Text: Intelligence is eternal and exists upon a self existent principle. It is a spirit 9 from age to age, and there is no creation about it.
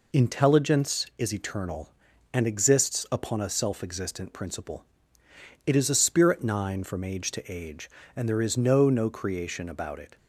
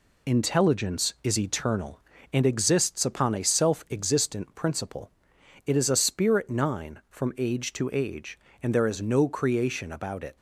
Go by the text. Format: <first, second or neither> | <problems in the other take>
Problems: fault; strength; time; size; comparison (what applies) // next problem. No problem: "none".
second | says "no" twice; at 8.8 s